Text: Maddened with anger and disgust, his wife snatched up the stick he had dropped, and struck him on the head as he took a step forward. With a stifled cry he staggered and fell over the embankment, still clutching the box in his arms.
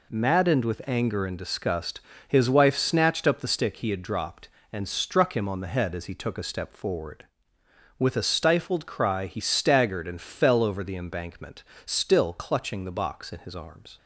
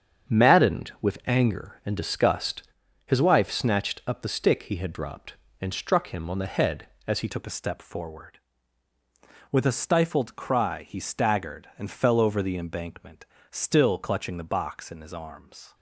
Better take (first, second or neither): first